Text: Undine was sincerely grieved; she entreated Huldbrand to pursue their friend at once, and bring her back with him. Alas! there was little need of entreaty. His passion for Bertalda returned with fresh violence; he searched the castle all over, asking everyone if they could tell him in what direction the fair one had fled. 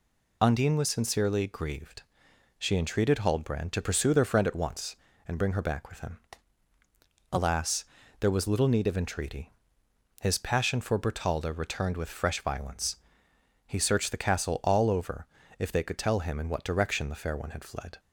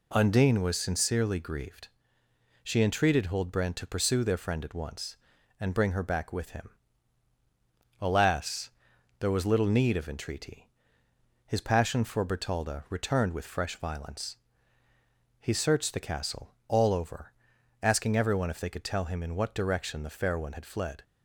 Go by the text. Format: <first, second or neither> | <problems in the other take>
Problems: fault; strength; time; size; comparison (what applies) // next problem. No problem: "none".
second | skips "asking everyone"; at 15.4 s